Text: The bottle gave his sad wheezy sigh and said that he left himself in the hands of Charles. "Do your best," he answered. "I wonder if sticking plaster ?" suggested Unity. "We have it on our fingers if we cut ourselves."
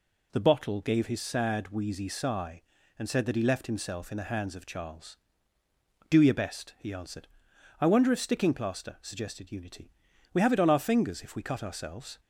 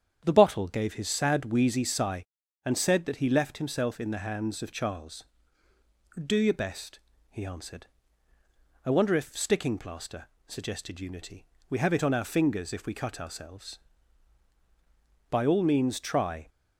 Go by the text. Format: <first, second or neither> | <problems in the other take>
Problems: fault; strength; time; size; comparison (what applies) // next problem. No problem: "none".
first | starts louder than the rest; strong; until 1.2 s; 8.5 dB // goes on to say "By all means try"; noticeable; from 15.3 s on; 1.1 s long